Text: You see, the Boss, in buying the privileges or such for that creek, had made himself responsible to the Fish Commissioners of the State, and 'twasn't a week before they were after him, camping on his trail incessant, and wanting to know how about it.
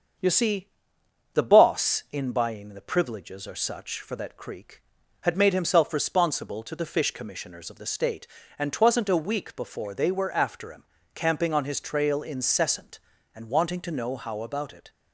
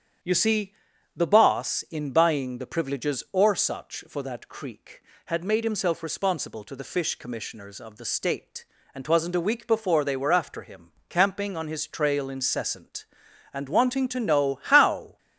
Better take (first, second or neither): first